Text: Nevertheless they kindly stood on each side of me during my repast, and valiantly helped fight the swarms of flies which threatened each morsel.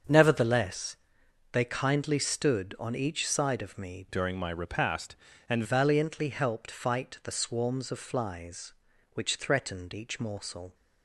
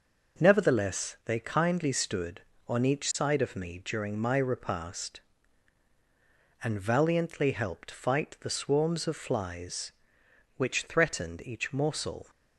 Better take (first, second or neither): second